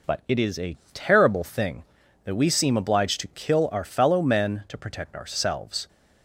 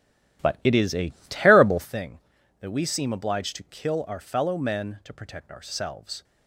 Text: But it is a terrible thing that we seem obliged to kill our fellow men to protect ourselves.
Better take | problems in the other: first | starts louder than the rest; strong; until 1.9 s; 13 dB // pauses between "a" and "terrible"; slight; at 1.1 s; 0.16 s long; slight in the first

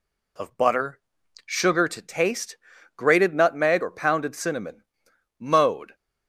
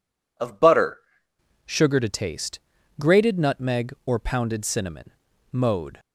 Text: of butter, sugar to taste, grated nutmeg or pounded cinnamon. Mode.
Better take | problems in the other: first | changes voice at "sugar"; from 1.6 s on; 4.3 s long

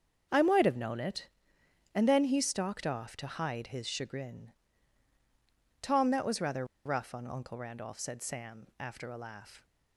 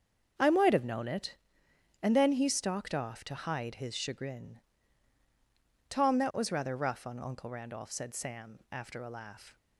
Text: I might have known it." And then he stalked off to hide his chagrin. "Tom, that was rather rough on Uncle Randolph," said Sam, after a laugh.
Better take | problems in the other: second | starts louder than the rest; until 1.9 s; 7 dB; also in the second // pauses between "rather" and "rough"; slight; at 6.6 s; 0.18 s long

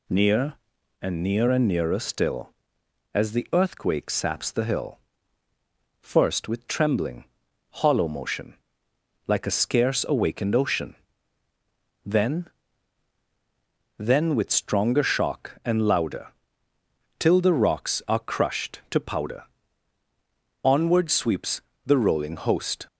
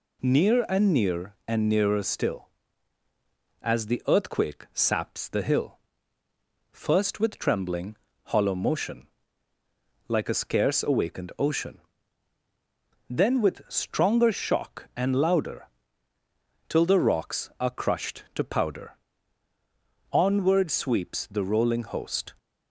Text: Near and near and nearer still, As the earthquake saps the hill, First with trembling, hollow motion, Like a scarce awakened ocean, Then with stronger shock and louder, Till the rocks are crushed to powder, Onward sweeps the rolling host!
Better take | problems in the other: second | says "Then" twice; at 13.9 s // pauses between "sweeps" and "the"; slight; at 21.6 s; 0.26 s long

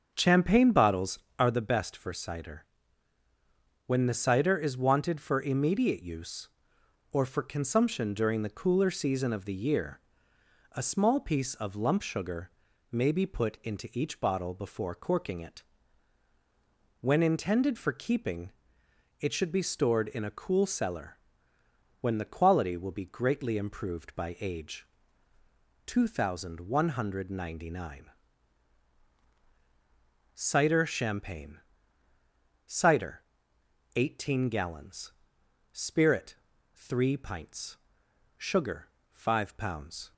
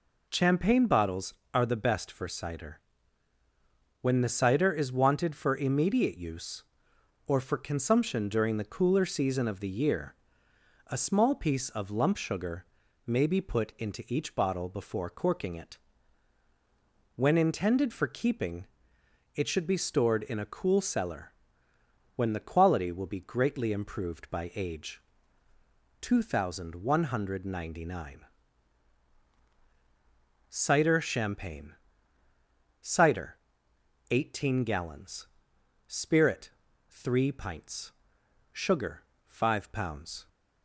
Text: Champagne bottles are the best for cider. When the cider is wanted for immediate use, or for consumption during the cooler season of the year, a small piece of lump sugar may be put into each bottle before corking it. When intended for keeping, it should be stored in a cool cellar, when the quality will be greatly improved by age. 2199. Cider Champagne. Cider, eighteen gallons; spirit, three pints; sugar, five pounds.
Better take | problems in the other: second | starts louder than the rest; until 1.7 s; 7 dB // pauses between "sugar" and "may"; at 12.5 s; 0.40 s long; also in the second

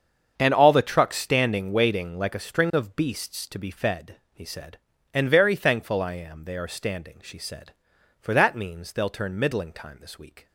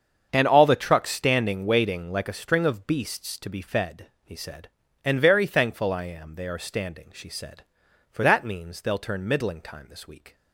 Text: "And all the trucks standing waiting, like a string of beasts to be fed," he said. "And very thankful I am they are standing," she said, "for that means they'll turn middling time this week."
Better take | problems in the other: neither | starts louder than the rest; strong; the same in both

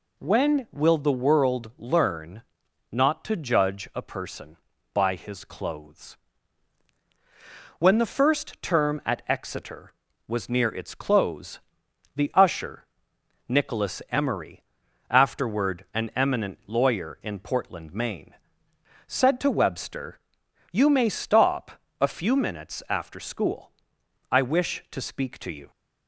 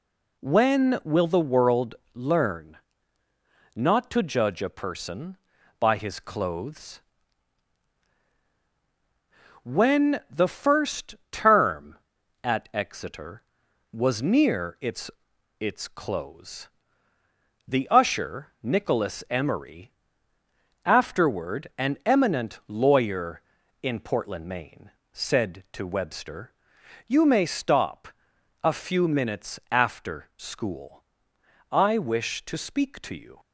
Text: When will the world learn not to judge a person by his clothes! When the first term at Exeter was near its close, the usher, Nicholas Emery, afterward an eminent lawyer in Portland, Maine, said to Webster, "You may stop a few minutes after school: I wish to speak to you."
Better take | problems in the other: first | pauses between "world" and "learn"; slight; at 1.9 s; 0.20 s long // pauses between "learn" and "not"; noticeable; at 2.7 s; 0.96 s long; noticeable in the first // pauses between "first" and "term"; slight; at 11.1 s; 0.16 s long // says "its" twice; at 15.5 s // pauses between "stop" and "a"; noticeable; at 28.0 s; 0.54 s long; slight in the first

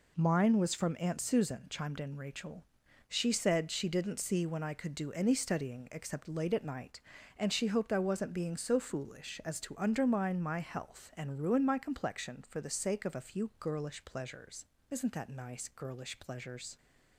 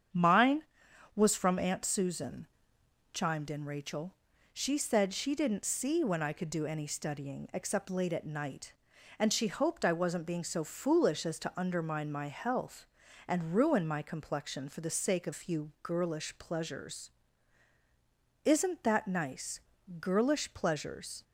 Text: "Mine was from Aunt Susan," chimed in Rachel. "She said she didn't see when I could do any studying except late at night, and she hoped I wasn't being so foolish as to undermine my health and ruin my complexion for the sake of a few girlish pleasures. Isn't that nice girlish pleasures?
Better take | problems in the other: first | starts louder than the rest; strong; until 1.6 s; 8 dB // skips "a"; at 15.3 s // pauses between "nice" and "girlish"; at 19.6 s; 0.38 s long

